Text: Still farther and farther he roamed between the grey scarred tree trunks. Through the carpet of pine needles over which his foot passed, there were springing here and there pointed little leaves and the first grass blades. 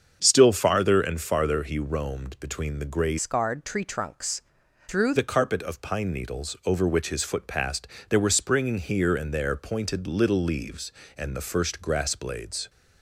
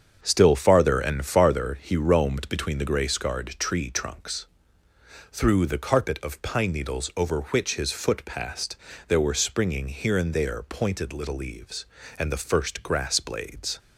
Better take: second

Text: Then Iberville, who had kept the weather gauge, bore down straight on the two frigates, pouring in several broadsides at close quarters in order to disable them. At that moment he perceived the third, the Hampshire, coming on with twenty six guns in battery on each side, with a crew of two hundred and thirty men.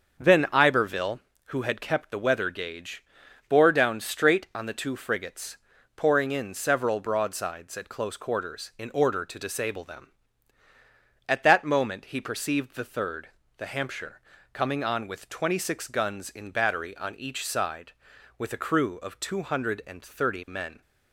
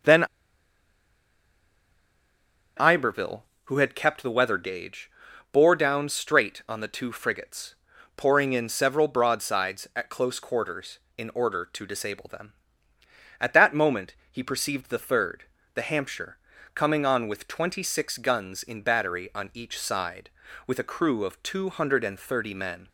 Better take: first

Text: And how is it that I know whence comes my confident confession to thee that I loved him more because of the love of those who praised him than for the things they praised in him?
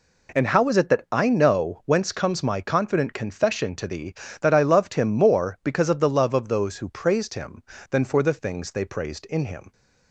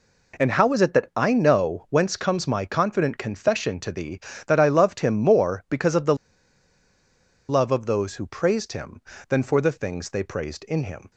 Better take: first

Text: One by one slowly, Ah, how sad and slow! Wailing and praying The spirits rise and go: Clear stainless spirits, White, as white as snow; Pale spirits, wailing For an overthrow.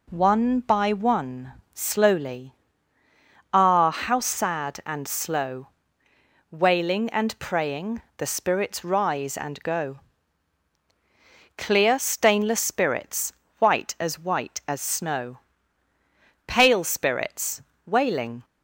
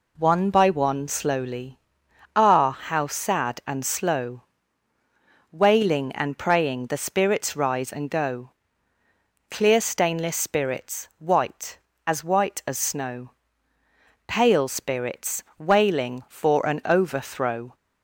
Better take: second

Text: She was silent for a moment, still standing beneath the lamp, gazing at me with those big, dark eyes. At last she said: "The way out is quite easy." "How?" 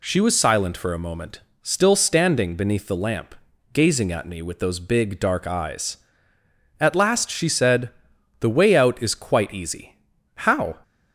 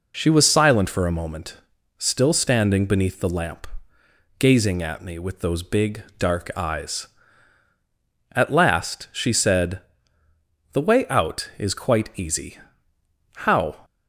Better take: neither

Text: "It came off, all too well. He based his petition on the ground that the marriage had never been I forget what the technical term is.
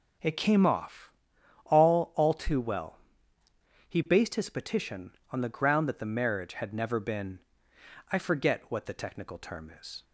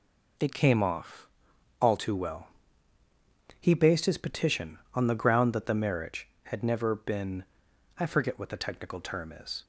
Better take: second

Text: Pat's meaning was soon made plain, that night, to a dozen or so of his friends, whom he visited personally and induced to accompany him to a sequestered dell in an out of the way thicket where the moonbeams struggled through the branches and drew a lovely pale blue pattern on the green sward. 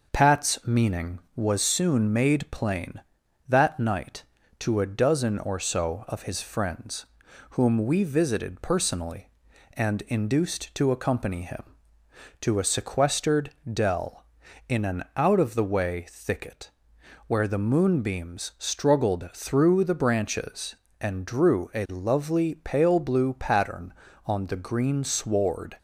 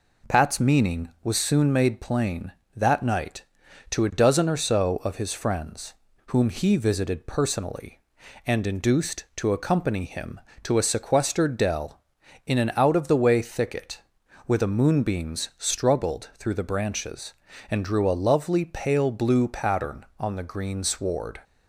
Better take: second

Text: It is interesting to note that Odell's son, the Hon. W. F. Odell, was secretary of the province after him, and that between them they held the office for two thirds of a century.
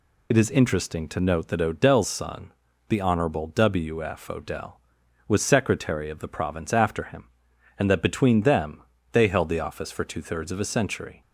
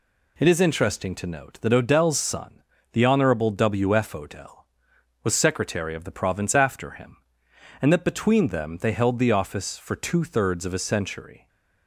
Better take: second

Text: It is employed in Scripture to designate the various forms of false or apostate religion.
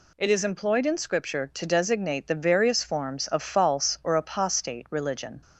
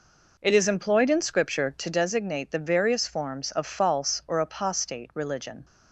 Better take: first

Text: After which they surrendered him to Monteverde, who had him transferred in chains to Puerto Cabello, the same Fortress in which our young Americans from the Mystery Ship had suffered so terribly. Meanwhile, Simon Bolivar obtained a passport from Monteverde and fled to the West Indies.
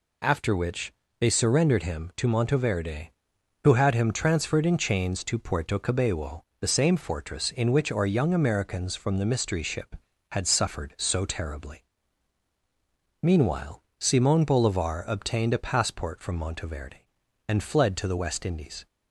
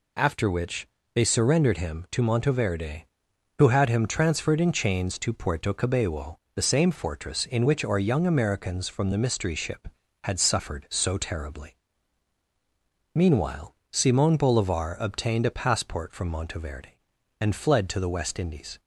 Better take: neither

